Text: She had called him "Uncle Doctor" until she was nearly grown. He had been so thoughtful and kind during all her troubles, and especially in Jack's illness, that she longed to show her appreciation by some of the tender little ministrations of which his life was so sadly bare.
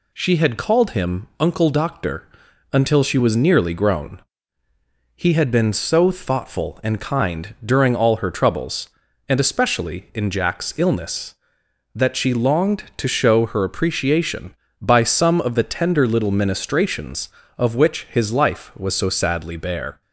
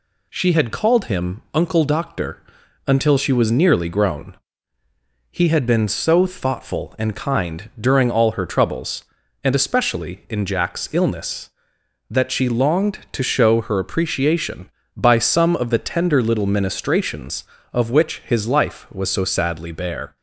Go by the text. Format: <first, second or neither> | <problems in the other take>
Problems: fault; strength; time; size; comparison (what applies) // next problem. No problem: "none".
neither | pauses between "Doctor" and "until"; the same in both